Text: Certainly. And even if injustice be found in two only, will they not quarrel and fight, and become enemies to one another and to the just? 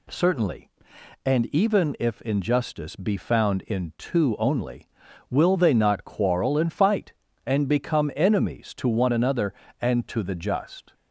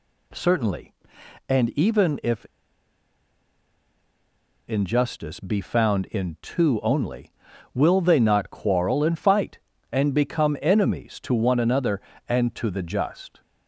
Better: first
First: none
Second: pauses between "if" and "injustice"; strong; at 2.4 s; 2.2 s long

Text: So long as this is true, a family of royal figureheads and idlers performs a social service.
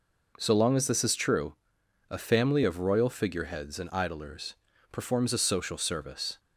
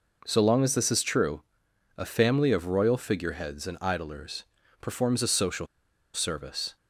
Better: first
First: pauses between "idlers" and "performs"; at 4.5 s; 0.38 s long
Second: pauses between "idlers" and "performs"; at 4.4 s; 0.38 s long // pauses between "social" and "service"; noticeable; at 5.6 s; 0.47 s long

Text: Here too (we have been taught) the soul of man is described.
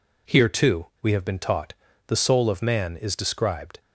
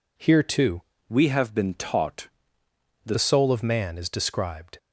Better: first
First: none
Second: changes voice from "we" to "the"; from 1.0 to 3.1 s; 2.1 s long

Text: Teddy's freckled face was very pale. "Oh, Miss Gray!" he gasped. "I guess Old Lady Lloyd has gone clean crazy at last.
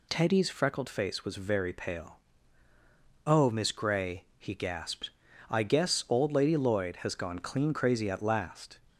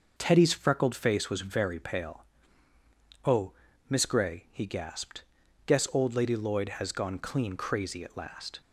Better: first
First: none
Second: starts louder than the rest; noticeable; until 1.1 s; 6 dB // skips "I"; at 5.4 s

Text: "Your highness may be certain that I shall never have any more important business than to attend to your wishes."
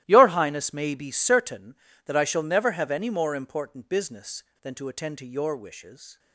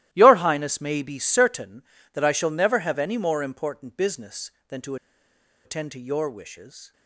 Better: first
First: starts louder than the rest; strong; until 1.0 s; 15 dB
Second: starts louder than the rest; strong; until 1.1 s; 15 dB // pauses between "to" and "attend"; noticeable; at 4.9 s; 0.69 s long

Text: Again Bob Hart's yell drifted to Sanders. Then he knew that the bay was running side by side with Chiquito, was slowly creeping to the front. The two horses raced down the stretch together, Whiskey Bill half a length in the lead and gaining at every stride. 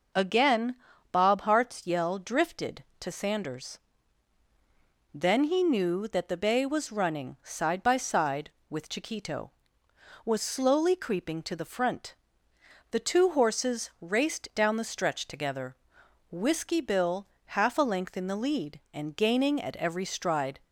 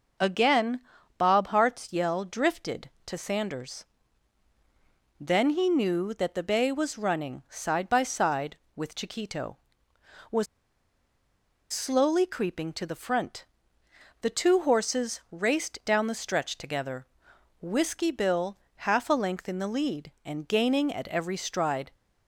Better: first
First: pauses between "Again" and "Bob"; at 0.7 s; 0.36 s long // pauses between "Bill" and "half"; slight; at 17.2 s; 0.26 s long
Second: pauses between "Again" and "Bob"; at 0.7 s; 0.38 s long // pauses between "was" and "slowly"; strong; at 10.4 s; 1.2 s long // pauses between "Bill" and "half"; slight; at 18.5 s; 0.26 s long

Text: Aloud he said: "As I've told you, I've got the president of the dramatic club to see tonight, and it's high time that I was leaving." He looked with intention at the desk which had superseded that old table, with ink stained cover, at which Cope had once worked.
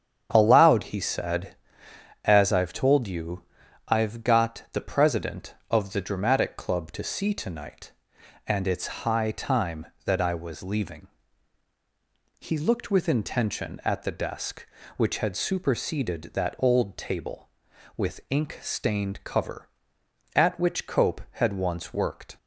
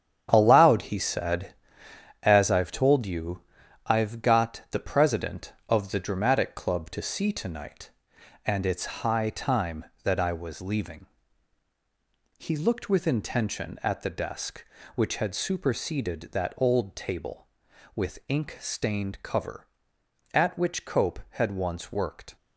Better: first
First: starts louder than the rest; strong; until 1.3 s; 8 dB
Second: gets quieter; strong; throughout; 7.5 dB // starts louder than the rest; strong; until 1.3 s; 9 dB

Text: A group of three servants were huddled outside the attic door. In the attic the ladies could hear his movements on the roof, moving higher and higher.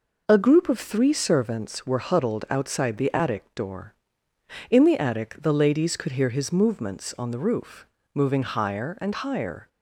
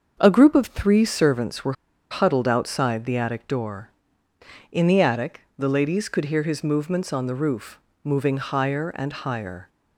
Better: first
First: none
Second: starts louder than the rest; until 1.1 s; 6.5 dB // pauses between "were" and "huddled"; at 1.7 s; 0.37 s long // pauses between "attic" and "the"; slight; at 5.4 s; 0.16 s long

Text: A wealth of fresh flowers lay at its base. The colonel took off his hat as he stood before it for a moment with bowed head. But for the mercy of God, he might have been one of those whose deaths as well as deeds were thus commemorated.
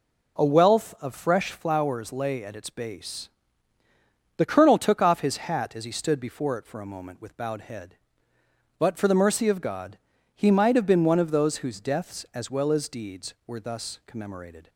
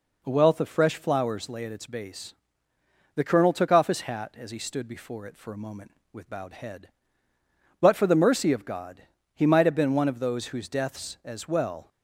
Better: first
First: none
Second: stops before "as deeds were thus commemorated"; at 11.8 s

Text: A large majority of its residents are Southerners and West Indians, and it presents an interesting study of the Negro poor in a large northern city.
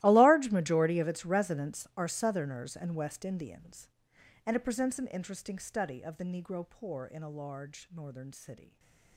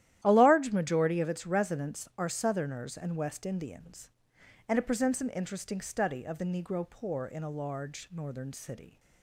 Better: second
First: gets quieter; strong; throughout; 20.5 dB // starts louder than the rest; strong; until 1.0 s; 16.5 dB // stays silent after the last word; slight; from 8.6 s on; 0.5 s long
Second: starts louder than the rest; strong; until 1.2 s; 12.5 dB

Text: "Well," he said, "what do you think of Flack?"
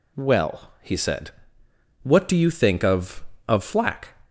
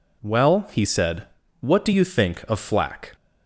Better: second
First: says "of" twice; at 3.4 s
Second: none

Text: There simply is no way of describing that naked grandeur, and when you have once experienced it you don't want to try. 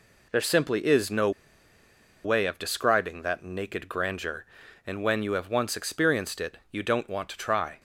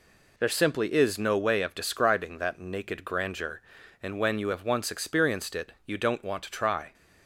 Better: second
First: pauses between "no" and "way"; noticeable; at 1.3 s; 0.94 s long // pauses between "it" and "you"; slight; at 6.5 s; 0.16 s long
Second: pauses between "it" and "you"; slight; at 5.7 s; 0.16 s long

